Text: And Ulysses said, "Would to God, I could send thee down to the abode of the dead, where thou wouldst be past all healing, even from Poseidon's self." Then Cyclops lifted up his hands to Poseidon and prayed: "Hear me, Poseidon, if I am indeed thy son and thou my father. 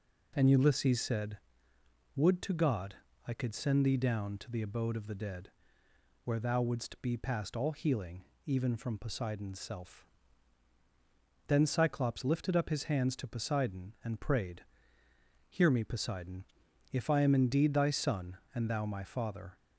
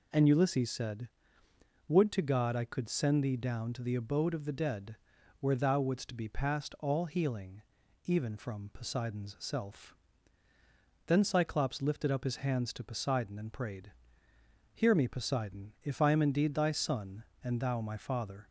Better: neither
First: none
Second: none

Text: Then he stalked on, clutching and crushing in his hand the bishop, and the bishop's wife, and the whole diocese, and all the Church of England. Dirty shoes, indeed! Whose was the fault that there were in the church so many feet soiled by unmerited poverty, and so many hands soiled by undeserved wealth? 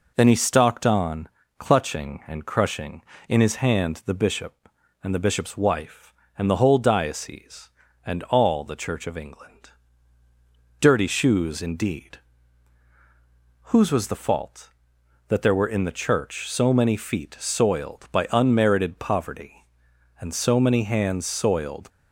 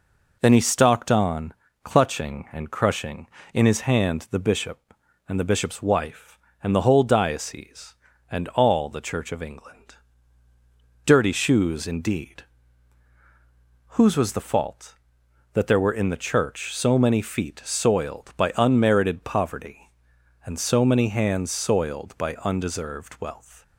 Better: second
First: stops before "by undeserved wealth"; at 21.8 s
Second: none

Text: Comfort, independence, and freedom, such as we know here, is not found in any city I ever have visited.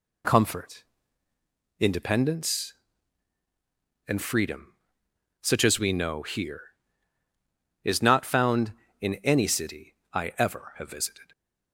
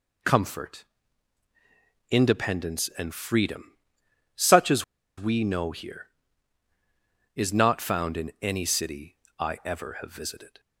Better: first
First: pauses between "city" and "I"; slight; at 9.9 s; 0.18 s long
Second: pauses between "as" and "we"; slight; at 4.8 s; 0.33 s long // pauses between "city" and "I"; slight; at 9.1 s; 0.24 s long

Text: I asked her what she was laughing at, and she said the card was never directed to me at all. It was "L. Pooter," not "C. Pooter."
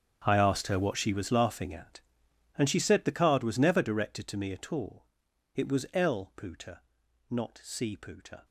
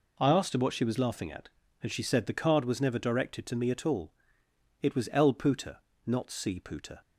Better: second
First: gets quieter; strong; throughout; 17.5 dB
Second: none

